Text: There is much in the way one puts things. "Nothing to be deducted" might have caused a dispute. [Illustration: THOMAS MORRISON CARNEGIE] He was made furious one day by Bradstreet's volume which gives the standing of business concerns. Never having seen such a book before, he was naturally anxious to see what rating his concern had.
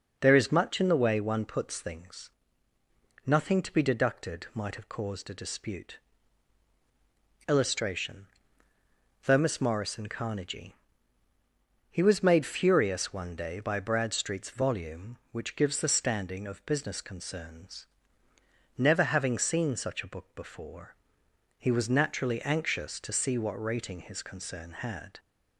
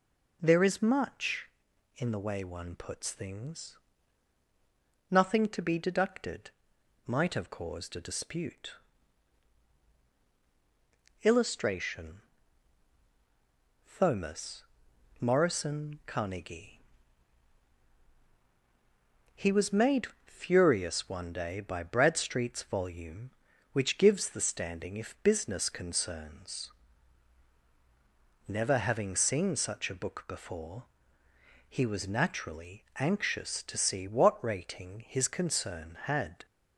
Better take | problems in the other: first | pauses between "deducted" and "might"; noticeable; at 6.5 s; 0.54 s long // pauses between "THOMAS" and "MORRISON"; noticeable; at 14.6 s; 0.56 s long // pauses between "CARNEGIE" and "He"; strong; at 16.7 s; 2.5 s long; also in the first // pauses between "made" and "furious"; slight; at 20.0 s; 0.18 s long // says "if" for "of"; at 24.9 s

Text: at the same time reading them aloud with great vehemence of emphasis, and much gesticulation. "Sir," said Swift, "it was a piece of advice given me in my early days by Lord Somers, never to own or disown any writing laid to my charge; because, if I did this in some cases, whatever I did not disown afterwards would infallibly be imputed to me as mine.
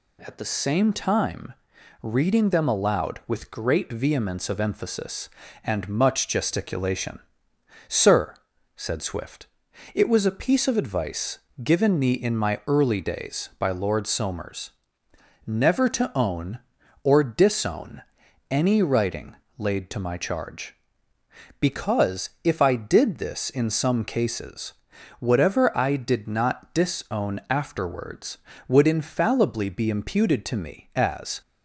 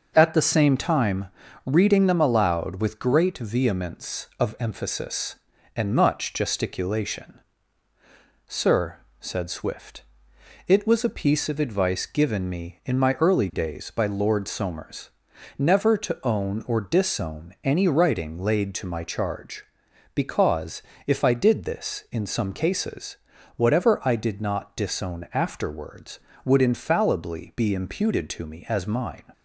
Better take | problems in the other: second | pauses between "time" and "reading"; noticeable; at 1.5 s; 0.48 s long; also in the second // pauses between "advice" and "given"; slight; at 11.3 s; 0.22 s long // pauses between "disown" and "any"; noticeable; at 18.0 s; 0.46 s long // pauses between "writing" and "laid"; slight; at 19.3 s; 0.22 s long // stops before "mine"; at 31.4 s

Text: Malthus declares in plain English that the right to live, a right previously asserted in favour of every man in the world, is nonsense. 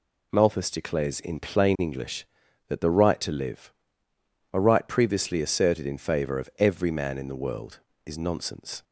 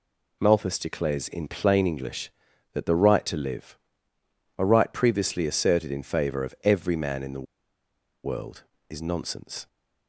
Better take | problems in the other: first | pauses between "the" and "world"; noticeable; at 7.4 s; 0.79 s long

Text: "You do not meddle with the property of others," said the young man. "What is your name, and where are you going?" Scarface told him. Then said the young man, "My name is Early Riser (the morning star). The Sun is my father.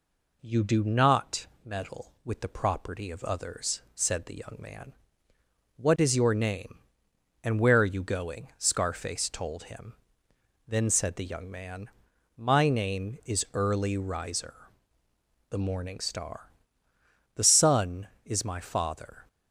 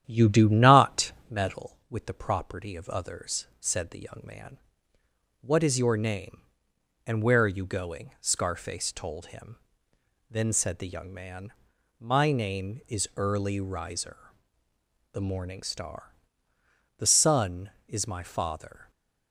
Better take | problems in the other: first | starts louder than the rest; strong; until 1.7 s; 10.5 dB // pauses between "not" and "meddle"; slight; at 1.1 s; 0.18 s long; slight in the first

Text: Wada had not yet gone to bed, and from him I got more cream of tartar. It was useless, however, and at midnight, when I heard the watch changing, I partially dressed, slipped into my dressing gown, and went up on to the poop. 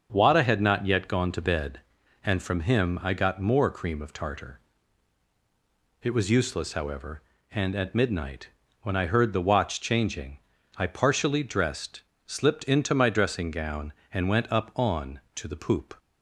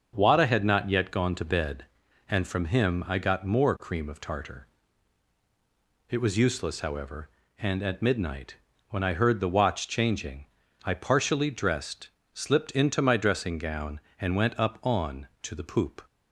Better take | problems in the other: neither | starts louder than the rest; the same in both

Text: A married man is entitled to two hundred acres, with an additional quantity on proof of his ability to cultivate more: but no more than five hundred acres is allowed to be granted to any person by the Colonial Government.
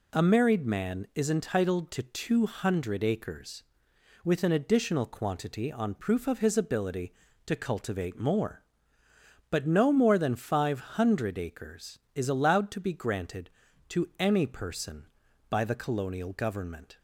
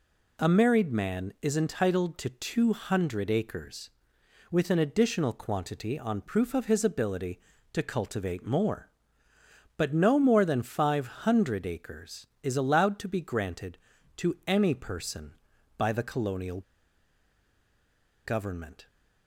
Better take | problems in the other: first | pauses between "Colonial" and "Government"; strong; at 16.6 s; 1.6 s long

